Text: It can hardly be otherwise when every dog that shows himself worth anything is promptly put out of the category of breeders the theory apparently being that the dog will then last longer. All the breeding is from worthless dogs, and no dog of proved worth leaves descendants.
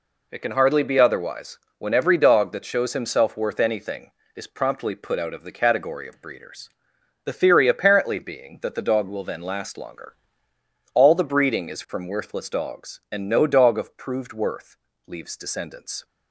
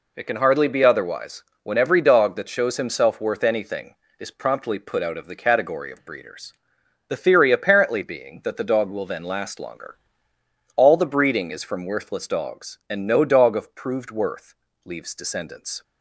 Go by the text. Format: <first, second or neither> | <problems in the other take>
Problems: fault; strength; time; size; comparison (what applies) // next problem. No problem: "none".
neither | pauses between "otherwise" and "when"; slight; the same in both // pauses between "breeders" and "the"; noticeable; the same in both // pauses between "worth" and "leaves"; slight; the same in both